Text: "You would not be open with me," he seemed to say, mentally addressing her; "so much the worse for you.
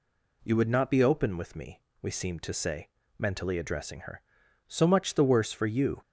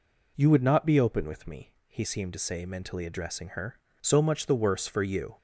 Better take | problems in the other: second | says "we" for "he"; at 2.0 s

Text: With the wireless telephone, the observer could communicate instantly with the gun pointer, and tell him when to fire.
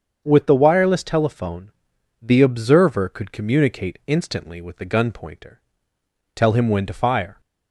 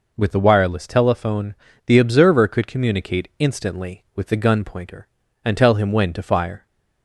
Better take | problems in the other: second | starts louder than the rest; strong; until 1.2 s; 7 dB // skips "and"; at 5.9 s

